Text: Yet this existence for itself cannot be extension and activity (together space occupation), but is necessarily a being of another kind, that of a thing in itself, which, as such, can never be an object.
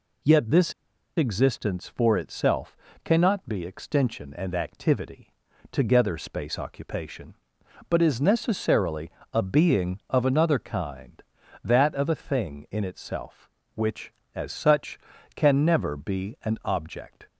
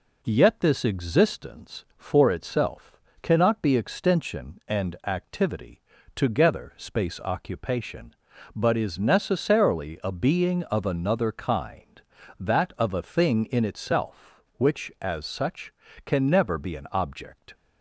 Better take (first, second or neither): second